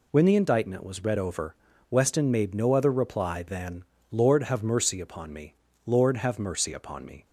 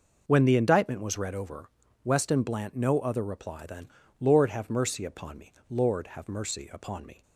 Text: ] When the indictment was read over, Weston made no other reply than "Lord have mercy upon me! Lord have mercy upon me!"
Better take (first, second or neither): first